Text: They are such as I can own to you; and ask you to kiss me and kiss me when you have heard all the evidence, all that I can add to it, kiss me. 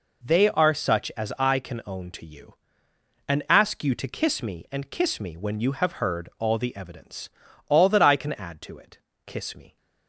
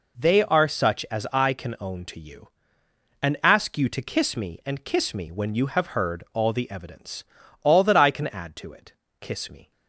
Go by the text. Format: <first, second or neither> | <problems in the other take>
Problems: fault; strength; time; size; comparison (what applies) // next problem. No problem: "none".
neither | none